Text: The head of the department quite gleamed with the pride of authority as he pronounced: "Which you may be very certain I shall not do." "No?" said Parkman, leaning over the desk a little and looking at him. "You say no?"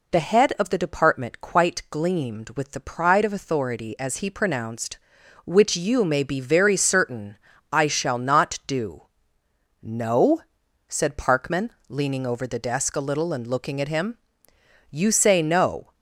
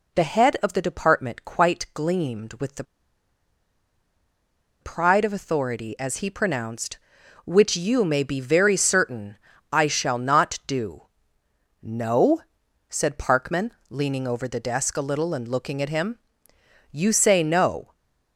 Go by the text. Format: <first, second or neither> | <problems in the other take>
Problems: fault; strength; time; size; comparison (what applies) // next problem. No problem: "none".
first | pauses between "the" and "pride"; strong; at 2.8 s; 1.9 s long // pauses between "certain" and "I"; slight; at 9.3 s; 0.34 s long; slight in the first // stays silent after the last word; slight; from 17.8 s on; 0.5 s long